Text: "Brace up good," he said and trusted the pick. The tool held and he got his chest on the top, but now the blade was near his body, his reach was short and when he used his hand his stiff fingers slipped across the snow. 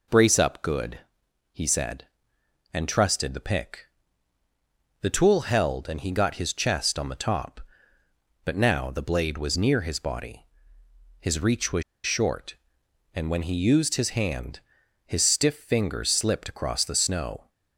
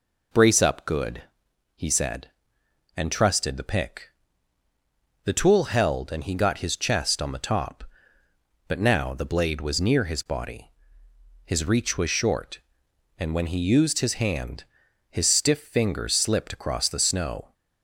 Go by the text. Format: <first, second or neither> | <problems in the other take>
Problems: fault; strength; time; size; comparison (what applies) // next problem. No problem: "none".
second | pauses between "was" and "short"; slight; at 11.8 s; 0.22 s long // pauses between "hand" and "his"; noticeable; at 14.5 s; 0.48 s long; noticeable in the second